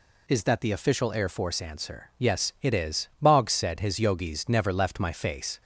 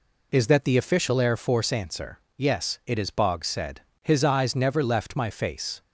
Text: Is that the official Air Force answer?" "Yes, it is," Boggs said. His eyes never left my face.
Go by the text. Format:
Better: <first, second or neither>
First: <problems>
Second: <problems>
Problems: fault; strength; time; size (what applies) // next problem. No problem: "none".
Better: second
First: says "yogis" for "eyes"; at 3.9 s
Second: none